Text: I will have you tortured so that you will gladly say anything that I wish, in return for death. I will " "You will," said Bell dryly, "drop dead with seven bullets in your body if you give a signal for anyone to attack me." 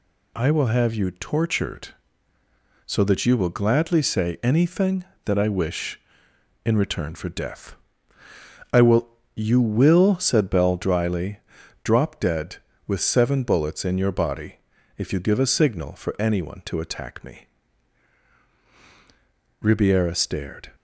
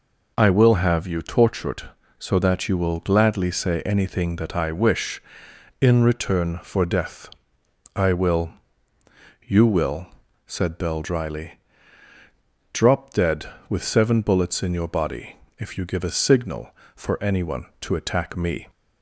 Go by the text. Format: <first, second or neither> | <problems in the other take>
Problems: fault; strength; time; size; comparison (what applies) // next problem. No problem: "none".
second | pauses between "body" and "if"; at 14.5 s; 0.40 s long; slight in the second // goes on to say "Ribiera stared"; noticeable; from 19.6 s on; 1.1 s long